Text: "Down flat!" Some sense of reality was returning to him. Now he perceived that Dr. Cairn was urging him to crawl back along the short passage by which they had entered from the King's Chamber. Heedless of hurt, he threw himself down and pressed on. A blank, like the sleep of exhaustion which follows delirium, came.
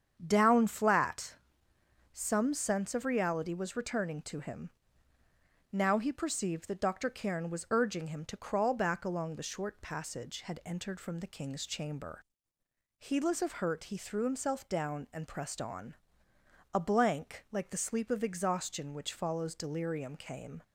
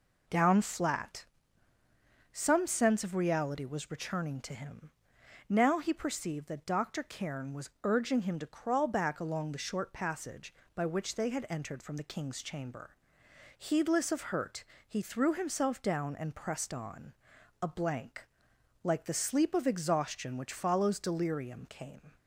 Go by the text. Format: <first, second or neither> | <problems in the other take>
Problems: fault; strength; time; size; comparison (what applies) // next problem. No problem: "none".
second | starts louder than the rest; strong; until 1.2 s; 8 dB // skips "by which they"; at 10.4 s